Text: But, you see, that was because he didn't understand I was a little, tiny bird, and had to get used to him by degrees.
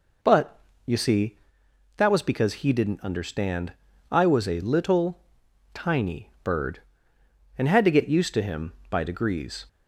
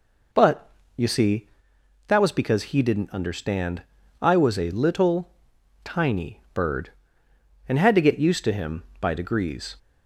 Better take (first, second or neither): neither